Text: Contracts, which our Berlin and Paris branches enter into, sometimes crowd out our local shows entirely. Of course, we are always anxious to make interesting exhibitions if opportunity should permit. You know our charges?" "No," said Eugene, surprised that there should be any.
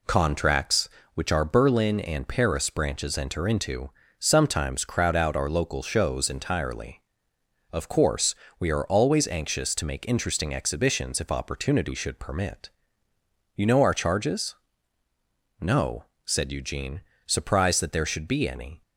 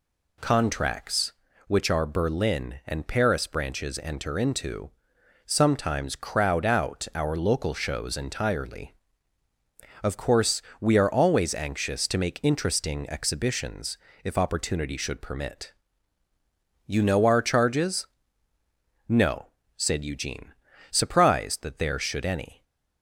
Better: first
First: none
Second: pauses between "exhibitions" and "if"; slight; at 13.9 s; 0.26 s long // skips "be"; at 22.2 s

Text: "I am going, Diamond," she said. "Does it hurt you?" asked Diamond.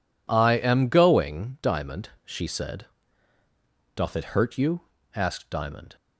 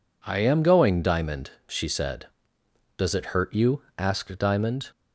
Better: second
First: says "Doth" for "Does"; at 3.9 s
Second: none

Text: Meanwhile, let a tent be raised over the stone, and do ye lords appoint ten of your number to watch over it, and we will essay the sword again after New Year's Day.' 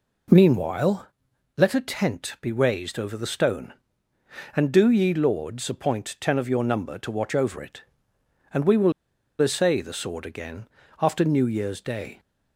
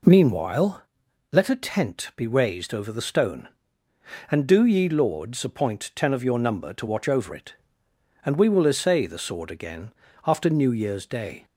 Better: second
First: pauses between "will" and "essay"; noticeable; at 8.9 s; 0.49 s long // pauses between "again" and "after"; slight; at 10.6 s; 0.34 s long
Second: pauses between "again" and "after"; slight; at 9.9 s; 0.34 s long

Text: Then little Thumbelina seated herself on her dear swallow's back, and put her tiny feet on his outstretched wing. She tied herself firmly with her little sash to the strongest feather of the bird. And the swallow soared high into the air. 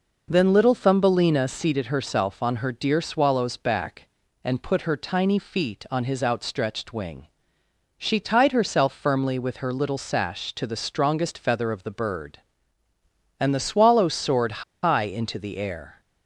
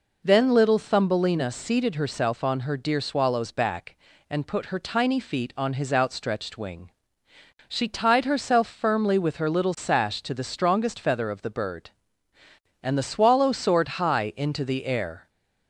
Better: second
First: pauses between "soared" and "high"; slight; at 14.6 s; 0.21 s long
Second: none

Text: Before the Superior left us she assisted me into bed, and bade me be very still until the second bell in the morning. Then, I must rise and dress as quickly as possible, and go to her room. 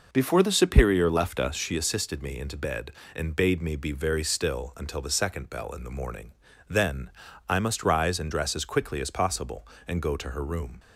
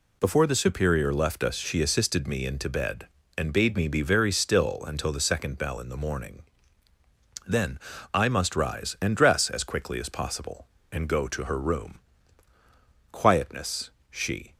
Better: first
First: none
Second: goes on to say "Quietness she"; from 13.1 s on; 1.4 s long

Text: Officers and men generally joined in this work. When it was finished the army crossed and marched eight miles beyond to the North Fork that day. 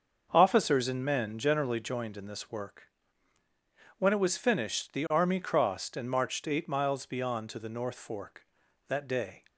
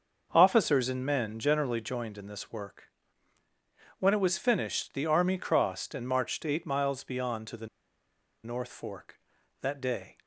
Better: first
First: starts louder than the rest; until 1.3 s; 6.5 dB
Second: starts louder than the rest; until 1.3 s; 6 dB // pauses between "the" and "North"; noticeable; at 7.6 s; 0.77 s long

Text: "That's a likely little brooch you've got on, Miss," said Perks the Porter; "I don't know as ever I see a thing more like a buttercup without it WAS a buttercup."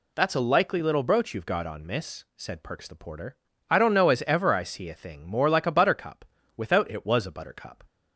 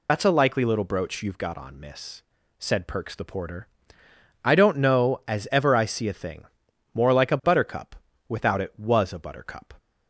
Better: first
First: pauses between "buttercup" and "without"; slight; at 6.2 s; 0.32 s long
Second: loses the start of "That's"; at 0.0 s; 50 ms // pauses between "thing" and "more"; noticeable; at 6.4 s; 0.50 s long // pauses between "buttercup" and "without"; slight; at 7.9 s; 0.32 s long

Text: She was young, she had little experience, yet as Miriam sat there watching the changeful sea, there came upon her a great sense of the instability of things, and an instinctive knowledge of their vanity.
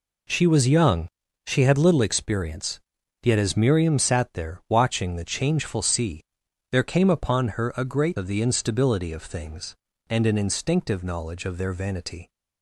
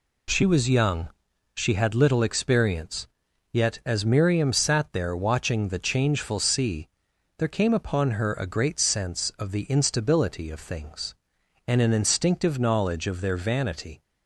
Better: second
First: skips "sense"; at 8.1 s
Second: none

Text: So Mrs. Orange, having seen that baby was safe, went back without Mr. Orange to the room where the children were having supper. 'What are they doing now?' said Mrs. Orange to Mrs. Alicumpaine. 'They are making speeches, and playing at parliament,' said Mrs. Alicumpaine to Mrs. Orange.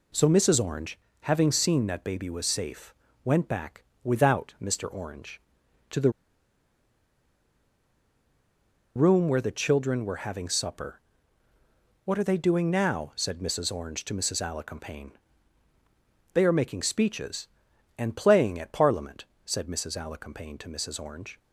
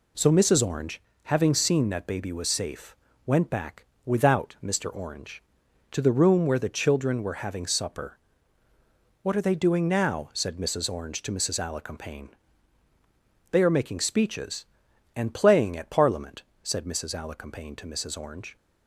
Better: second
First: pauses between "back" and "without"; slight; at 3.8 s; 0.22 s long // pauses between "the" and "room"; strong; at 6.1 s; 2.8 s long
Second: pauses between "back" and "without"; slight; at 3.8 s; 0.22 s long

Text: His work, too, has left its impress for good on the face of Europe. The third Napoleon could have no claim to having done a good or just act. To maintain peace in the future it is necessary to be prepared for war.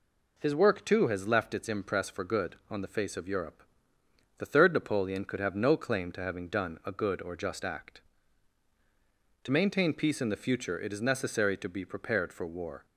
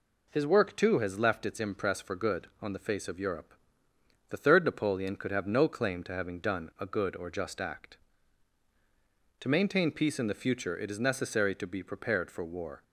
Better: neither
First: none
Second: none

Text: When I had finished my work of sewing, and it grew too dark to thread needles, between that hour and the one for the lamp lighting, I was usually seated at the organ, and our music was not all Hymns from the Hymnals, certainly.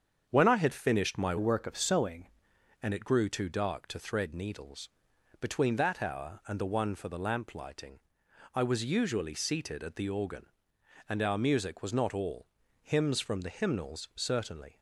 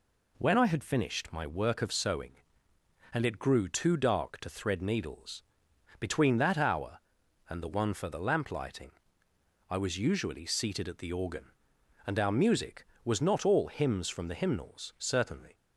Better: second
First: starts louder than the rest; strong; until 1.3 s; 7.5 dB // changes voice from "work" to "sewing"; from 1.3 to 2.2 s; 0.9 s long // pauses between "all" and "Hymns"; slight; at 12.4 s; 0.36 s long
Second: none

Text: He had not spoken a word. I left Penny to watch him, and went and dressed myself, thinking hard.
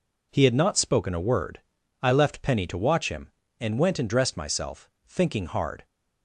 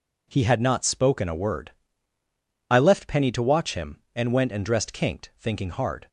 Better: first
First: none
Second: says "kinked" for "myself"; at 4.9 s

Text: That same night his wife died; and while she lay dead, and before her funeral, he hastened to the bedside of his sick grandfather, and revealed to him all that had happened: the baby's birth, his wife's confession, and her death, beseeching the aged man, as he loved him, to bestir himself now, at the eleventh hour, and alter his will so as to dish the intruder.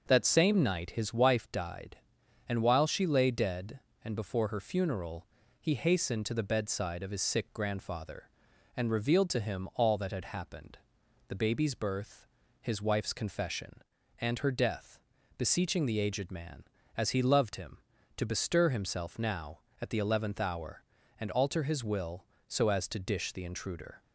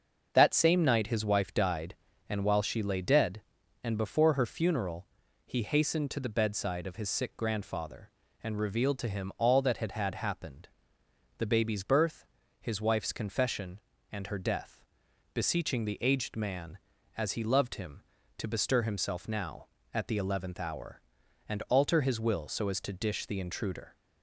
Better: first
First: starts louder than the rest; until 1.0 s; 6.5 dB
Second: starts louder than the rest; until 1.3 s; 6.5 dB // says "had" twice; at 9.9 s

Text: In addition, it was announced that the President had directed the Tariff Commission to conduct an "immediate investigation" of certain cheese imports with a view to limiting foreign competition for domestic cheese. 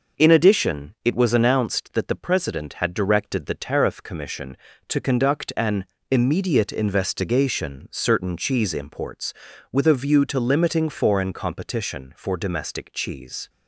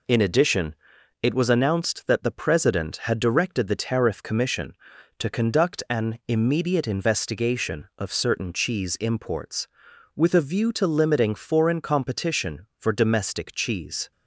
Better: second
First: pauses between "an" and "immediate"; slight; at 5.8 s; 0.26 s long // skips "of"; at 7.9 s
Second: none

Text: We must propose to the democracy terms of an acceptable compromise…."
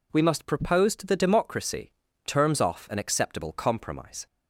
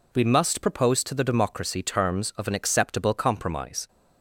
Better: second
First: pauses between "democracy" and "terms"; slight; at 1.9 s; 0.34 s long // says "off" for "of"; at 2.5 s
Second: none

